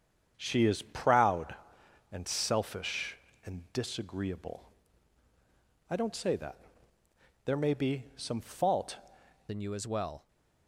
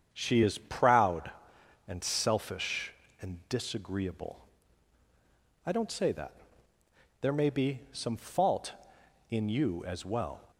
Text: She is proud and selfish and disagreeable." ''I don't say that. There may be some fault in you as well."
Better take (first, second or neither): second